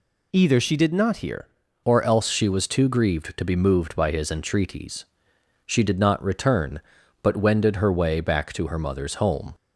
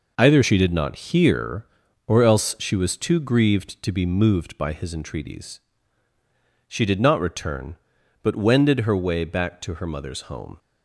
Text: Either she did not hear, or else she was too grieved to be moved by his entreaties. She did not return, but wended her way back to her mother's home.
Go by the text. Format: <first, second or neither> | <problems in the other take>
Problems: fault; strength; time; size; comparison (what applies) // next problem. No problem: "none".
second | changes voice at "or"; from 1.8 s on; 7.7 s long